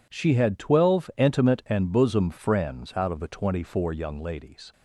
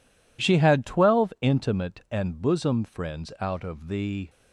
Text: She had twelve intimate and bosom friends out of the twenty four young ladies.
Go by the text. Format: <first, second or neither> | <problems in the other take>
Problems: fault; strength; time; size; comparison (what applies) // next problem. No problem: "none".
first | stops before "twenty four young ladies"; at 4.2 s